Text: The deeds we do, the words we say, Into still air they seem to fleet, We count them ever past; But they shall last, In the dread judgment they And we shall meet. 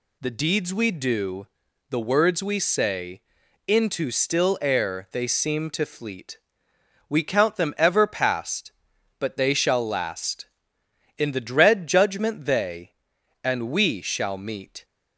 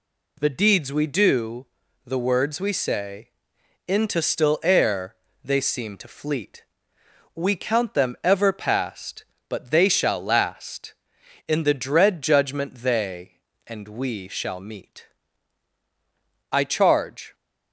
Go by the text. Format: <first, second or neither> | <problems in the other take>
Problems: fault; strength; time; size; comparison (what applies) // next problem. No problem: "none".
first | pauses between "air" and "they"; slight; at 5.1 s; 0.26 s long // goes on to say "I charge"; noticeable; from 16.5 s on; 0.82 s long